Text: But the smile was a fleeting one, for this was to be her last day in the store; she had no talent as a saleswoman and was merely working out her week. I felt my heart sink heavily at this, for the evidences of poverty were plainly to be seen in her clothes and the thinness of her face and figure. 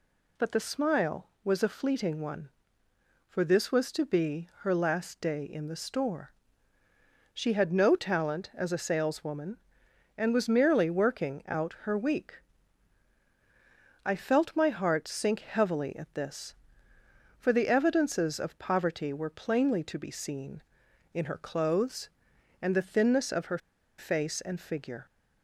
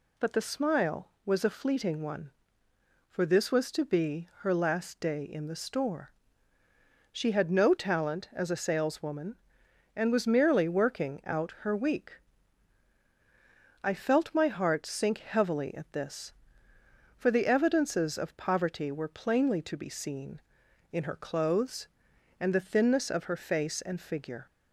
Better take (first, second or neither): second